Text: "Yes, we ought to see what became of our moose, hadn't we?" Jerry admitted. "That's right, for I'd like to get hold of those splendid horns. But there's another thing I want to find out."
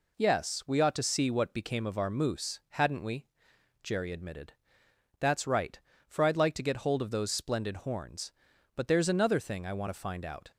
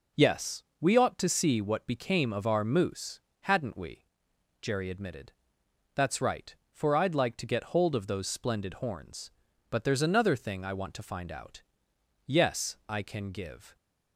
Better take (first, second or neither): first